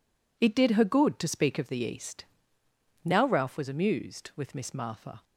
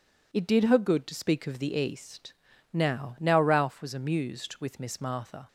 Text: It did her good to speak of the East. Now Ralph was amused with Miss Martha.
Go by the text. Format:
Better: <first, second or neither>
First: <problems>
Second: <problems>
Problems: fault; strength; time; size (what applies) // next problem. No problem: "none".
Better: first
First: none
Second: says "Now" twice; at 3.1 s